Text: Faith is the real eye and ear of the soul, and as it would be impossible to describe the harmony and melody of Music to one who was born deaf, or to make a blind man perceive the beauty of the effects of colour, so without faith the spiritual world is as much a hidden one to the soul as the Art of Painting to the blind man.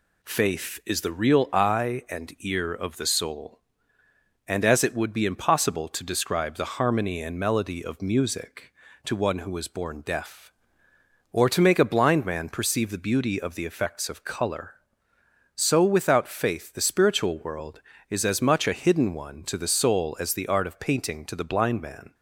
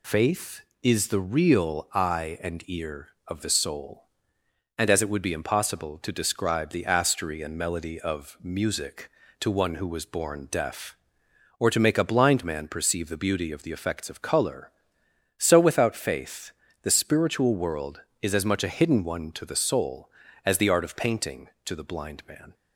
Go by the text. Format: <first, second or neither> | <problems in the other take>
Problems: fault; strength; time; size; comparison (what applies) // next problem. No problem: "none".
first | says "astery" for "harmony"; at 6.8 s // pauses between "faith" and "the"; slight; at 16.5 s; 0.32 s long